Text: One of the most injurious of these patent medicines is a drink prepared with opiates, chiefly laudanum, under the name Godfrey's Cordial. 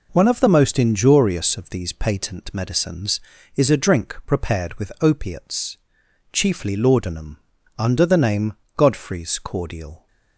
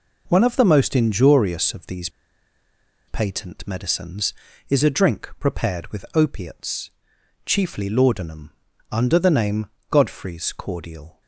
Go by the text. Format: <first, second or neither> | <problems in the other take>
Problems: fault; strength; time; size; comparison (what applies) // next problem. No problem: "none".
first | pauses between "these" and "patent"; at 2.0 s; 0.99 s long // pauses between "name" and "Godfrey's"; slight; at 9.6 s; 0.22 s long; slight in the first